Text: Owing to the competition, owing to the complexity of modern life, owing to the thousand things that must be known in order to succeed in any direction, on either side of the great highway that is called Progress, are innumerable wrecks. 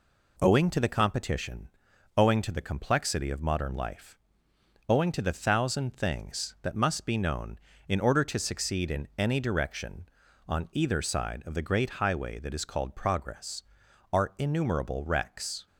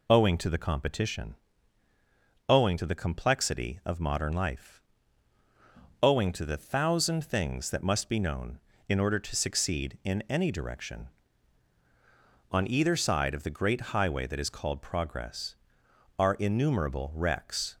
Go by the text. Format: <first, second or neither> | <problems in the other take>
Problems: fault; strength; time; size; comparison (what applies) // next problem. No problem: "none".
neither | none